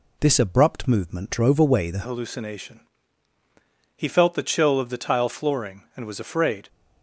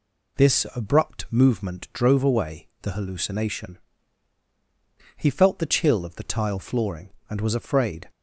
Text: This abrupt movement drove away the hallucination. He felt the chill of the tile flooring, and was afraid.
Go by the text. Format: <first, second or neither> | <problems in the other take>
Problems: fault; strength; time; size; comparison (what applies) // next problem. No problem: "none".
second | changes voice at "hallucination"; from 2.0 s on; 4.6 s long